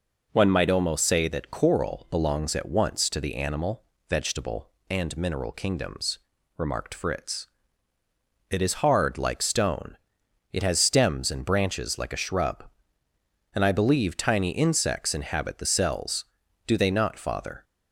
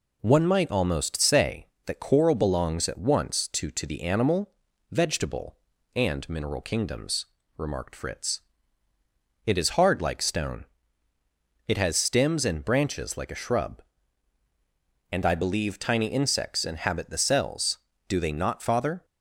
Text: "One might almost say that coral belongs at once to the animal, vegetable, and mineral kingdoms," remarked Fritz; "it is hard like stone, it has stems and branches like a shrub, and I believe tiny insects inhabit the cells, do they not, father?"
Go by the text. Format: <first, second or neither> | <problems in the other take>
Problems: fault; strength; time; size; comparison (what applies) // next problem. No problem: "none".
first | says "to" twice; at 3.7 s